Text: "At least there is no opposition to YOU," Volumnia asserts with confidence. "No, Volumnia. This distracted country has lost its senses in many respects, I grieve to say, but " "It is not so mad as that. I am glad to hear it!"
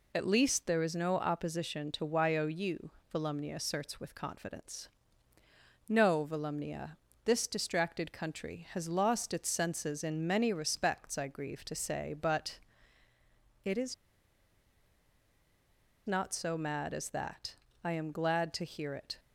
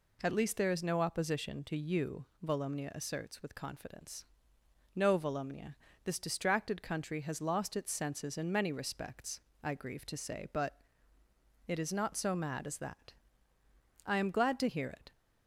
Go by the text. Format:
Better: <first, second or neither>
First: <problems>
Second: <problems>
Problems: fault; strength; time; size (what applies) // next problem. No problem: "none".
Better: second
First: pauses between "is" and "not"; strong; at 13.9 s; 2.1 s long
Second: none